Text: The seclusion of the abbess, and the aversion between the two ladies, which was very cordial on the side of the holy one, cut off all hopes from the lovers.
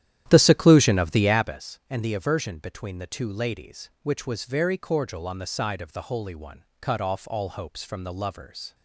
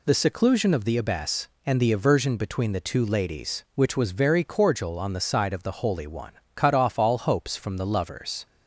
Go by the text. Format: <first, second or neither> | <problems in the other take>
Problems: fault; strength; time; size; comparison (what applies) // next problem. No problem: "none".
second | starts louder than the rest; strong; until 1.6 s; 11.5 dB